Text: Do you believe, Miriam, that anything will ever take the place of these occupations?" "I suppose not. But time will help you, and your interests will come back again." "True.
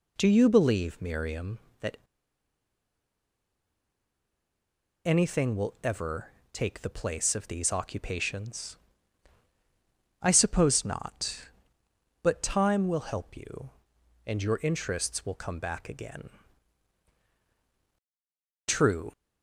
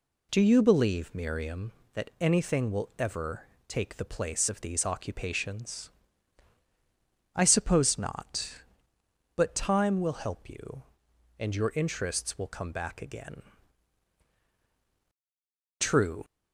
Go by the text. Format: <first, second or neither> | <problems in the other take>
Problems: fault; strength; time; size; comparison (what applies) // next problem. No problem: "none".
second | pauses between "that" and "anything"; strong; at 1.9 s; 3.0 s long // pauses between "ever" and "take"; slight; at 6.3 s; 0.20 s long; slight in the second